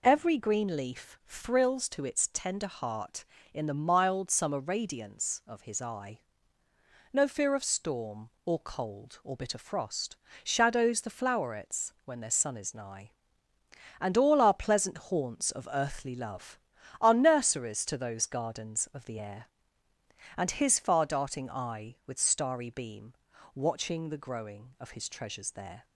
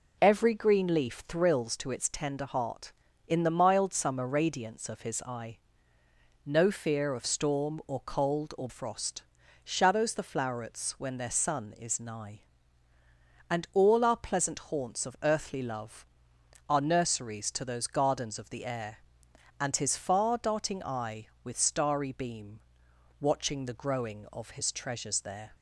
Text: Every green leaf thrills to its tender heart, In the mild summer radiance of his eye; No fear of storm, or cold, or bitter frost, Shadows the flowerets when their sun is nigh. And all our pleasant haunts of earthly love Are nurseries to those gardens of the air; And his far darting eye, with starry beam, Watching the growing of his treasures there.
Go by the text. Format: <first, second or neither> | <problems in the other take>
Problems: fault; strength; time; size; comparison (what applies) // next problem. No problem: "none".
first | skips "bitter"; at 8.6 s